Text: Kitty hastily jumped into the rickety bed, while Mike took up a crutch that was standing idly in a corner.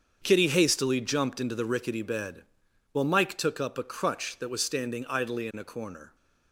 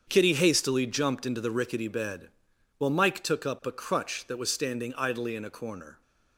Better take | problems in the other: neither | starts louder than the rest; strong; the same in both

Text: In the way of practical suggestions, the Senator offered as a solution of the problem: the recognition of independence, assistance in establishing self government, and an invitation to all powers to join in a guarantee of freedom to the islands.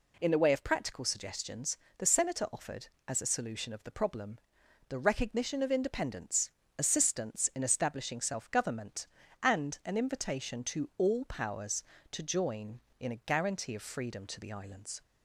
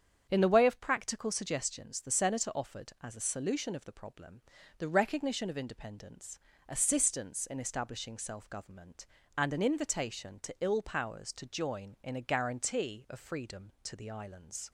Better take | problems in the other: first | starts louder than the rest; strong; until 1.3 s; 8 dB // says "ill" for "all"; at 10.6 s

